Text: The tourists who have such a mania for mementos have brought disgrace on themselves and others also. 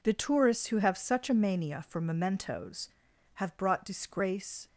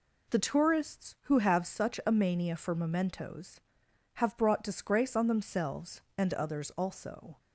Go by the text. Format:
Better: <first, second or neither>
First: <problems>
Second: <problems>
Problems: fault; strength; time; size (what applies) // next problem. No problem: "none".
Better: second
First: stops before "on themselves and others also"; at 4.6 s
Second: none